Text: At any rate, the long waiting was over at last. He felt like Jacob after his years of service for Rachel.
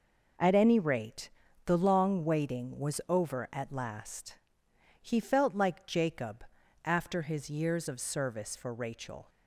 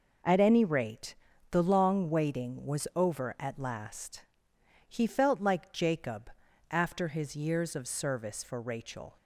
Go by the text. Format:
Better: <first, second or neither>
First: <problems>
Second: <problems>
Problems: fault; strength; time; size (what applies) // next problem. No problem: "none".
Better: neither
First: pauses between "Jacob" and "after"; at 6.4 s; 0.40 s long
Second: pauses between "Jacob" and "after"; at 6.3 s; 0.40 s long